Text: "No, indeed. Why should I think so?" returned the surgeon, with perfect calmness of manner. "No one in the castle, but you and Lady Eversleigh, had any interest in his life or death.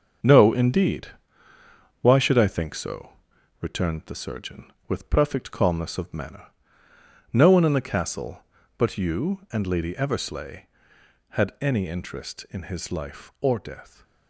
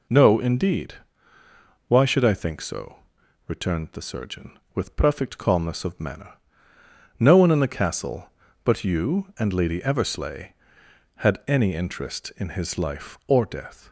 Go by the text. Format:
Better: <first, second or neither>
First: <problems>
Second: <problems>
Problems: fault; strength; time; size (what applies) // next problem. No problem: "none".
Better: second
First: gets quieter; strong; throughout; 8 dB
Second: none